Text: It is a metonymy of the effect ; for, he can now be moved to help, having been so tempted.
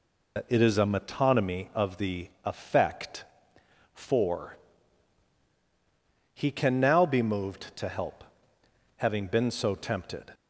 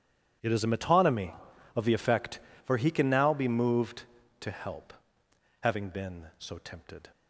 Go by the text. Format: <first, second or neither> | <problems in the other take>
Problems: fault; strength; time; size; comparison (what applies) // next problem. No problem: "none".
second | loses the start of "It"; at 0.3 s; 60 ms // pauses between "the" and "effect"; slight; at 2.2 s; 0.16 s long